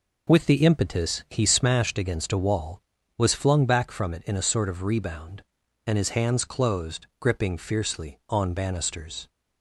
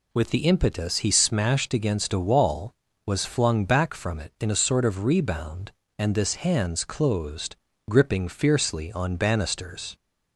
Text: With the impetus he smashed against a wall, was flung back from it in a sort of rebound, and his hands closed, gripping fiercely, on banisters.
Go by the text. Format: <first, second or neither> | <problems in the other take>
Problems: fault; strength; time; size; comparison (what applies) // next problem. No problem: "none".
first | says "this" for "his"; at 6.1 s